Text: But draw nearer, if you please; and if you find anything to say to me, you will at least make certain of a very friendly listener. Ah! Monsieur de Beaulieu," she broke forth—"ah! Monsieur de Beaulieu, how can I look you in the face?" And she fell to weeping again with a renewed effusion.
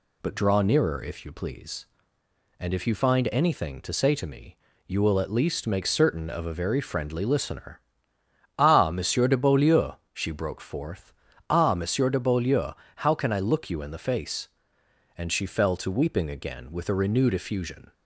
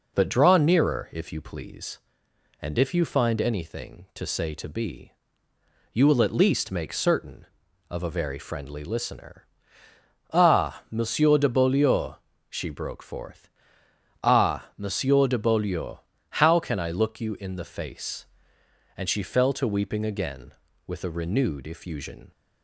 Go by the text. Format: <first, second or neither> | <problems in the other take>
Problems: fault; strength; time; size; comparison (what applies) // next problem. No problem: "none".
first | says "be" for "me"; at 4.6 s